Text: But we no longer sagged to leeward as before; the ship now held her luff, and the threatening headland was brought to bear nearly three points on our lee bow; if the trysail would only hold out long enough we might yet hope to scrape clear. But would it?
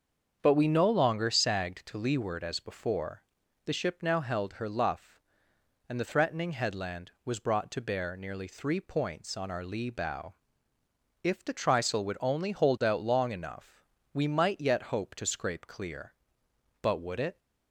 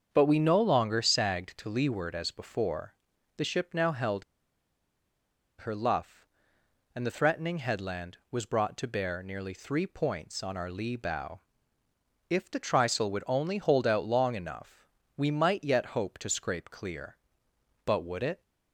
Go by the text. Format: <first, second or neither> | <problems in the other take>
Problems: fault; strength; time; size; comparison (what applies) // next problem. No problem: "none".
first | starts louder than the rest; until 1.1 s; 7 dB; strong in the first // pauses between "held" and "her"; strong; at 4.2 s; 1.3 s long // pauses between "enough" and "we"; slight; at 14.8 s; 0.28 s long; slight in the first